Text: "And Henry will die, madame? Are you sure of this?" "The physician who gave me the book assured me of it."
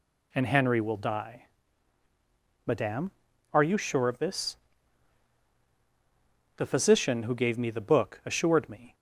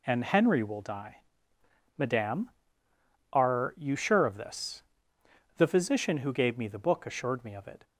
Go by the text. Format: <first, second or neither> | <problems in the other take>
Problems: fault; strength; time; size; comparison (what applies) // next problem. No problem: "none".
second | stops before "of it"; at 8.9 s